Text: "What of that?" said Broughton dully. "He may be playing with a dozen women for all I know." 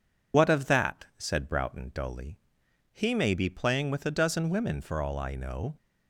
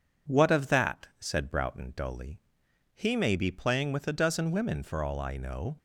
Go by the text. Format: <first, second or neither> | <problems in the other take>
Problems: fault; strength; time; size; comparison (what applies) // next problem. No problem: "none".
second | loses the start of "What"; at 0.3 s; 95 ms